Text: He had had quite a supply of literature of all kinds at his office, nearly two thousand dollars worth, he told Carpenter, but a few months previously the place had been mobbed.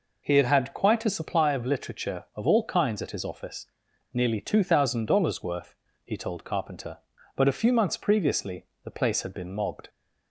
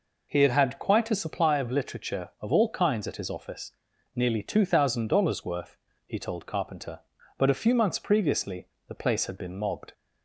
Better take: neither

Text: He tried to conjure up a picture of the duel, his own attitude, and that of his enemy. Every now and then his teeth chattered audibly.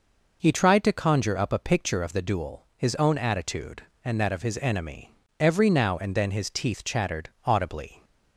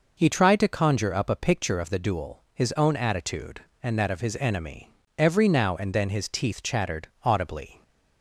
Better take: neither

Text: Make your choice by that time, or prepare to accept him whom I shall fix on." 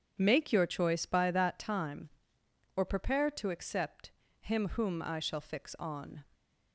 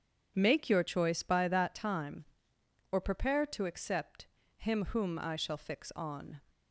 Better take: neither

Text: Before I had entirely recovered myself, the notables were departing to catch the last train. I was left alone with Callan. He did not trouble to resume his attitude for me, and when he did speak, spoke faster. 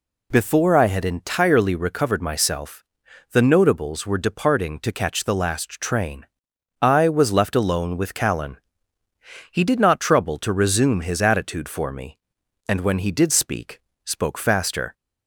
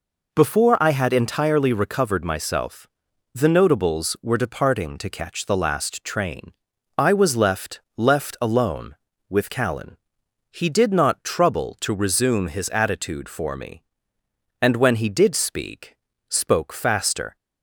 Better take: first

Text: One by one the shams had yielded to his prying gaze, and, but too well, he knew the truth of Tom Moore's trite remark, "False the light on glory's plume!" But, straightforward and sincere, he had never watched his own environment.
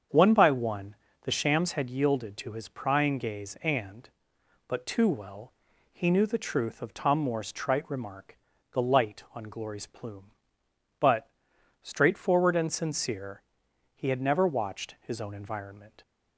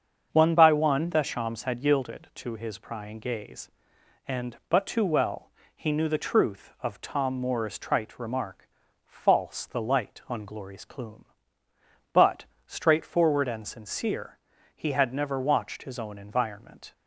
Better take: second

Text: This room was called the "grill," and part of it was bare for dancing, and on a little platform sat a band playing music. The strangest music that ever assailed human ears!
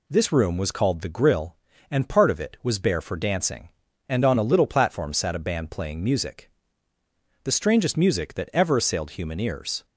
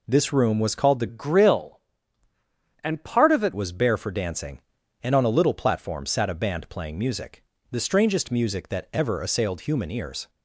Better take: first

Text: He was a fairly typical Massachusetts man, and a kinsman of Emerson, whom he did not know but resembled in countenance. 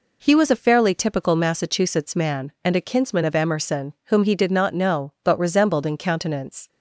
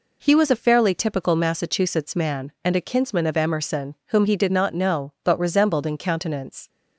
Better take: neither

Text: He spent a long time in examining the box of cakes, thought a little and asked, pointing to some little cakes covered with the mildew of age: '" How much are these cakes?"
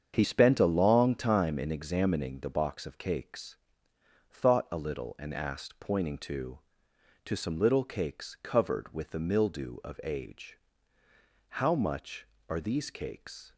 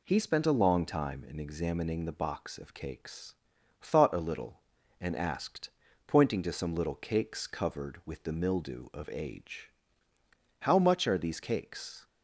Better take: second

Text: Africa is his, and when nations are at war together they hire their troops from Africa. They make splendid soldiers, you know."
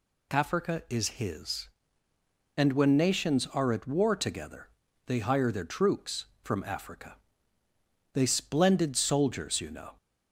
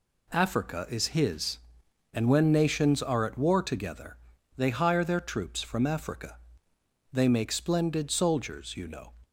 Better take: second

